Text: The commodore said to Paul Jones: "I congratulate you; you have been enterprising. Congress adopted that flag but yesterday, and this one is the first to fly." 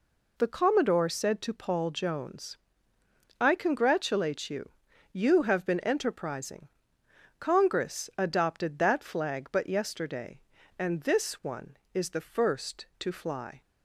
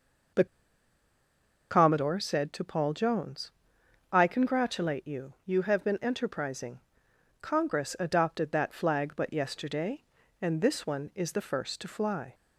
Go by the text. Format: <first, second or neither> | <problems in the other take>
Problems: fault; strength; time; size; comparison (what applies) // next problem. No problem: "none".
first | pauses between "The" and "commodore"; strong; at 0.4 s; 1.2 s long